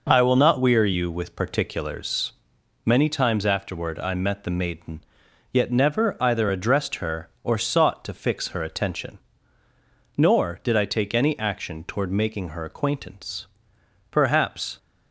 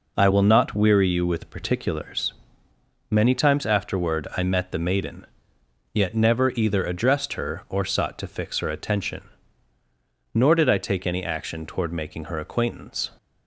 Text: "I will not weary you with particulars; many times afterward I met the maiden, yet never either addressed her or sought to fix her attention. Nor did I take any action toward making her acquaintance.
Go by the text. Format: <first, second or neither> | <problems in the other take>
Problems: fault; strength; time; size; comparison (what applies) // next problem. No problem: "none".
second | goes on to say "Perhaps"; noticeable; from 14.1 s on; 0.66 s long